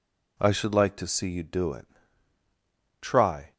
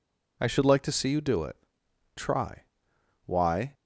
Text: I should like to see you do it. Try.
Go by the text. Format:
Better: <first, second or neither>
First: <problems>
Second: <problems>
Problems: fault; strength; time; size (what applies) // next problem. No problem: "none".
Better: first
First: none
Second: goes on to say "Why"; slight; from 3.2 s on; 0.48 s long